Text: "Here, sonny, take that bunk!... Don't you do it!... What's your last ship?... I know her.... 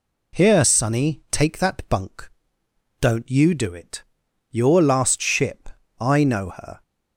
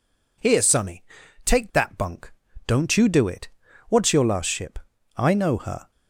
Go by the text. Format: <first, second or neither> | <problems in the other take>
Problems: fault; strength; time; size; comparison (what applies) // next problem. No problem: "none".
second | skips "What's"; at 4.2 s